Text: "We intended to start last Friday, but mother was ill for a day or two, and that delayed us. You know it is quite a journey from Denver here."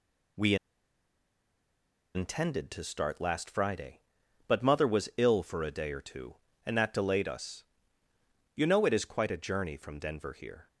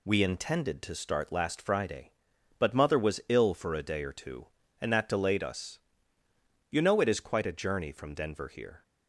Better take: second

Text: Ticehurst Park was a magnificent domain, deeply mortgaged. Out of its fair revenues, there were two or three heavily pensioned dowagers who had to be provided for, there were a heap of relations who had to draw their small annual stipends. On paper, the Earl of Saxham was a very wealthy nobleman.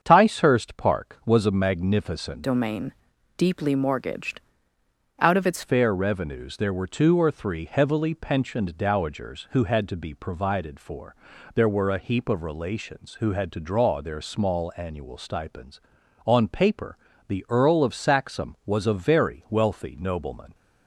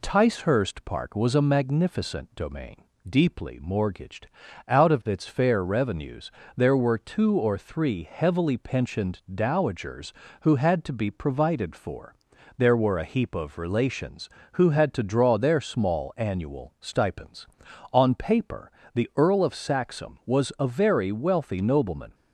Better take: second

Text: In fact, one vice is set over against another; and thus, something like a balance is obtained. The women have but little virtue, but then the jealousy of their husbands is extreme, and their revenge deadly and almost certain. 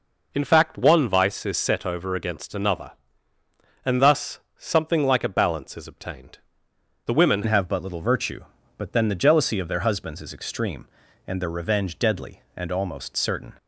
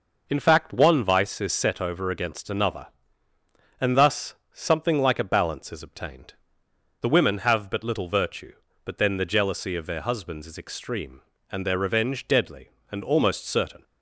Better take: second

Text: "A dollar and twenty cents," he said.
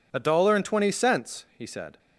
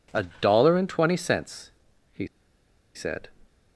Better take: first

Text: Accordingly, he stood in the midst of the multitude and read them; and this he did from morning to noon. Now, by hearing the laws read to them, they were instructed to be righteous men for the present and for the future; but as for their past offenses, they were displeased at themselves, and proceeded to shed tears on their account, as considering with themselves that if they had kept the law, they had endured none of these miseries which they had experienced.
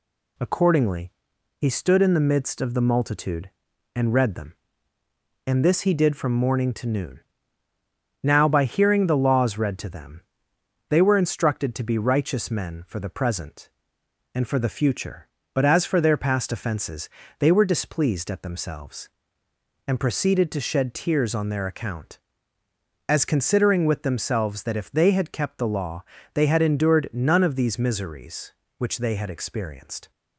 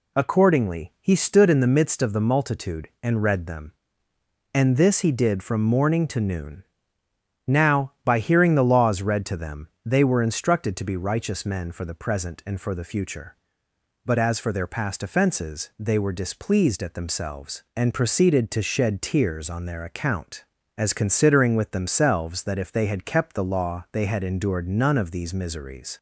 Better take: first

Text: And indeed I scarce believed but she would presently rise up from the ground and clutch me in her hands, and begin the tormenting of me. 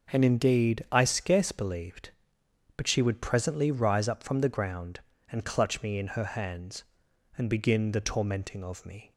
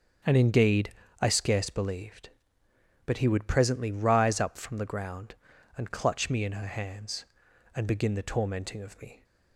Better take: first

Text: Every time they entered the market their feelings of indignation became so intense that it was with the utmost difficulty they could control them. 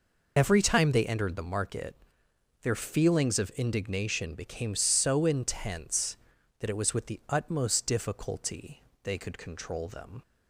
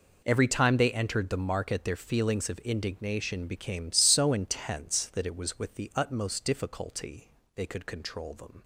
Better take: second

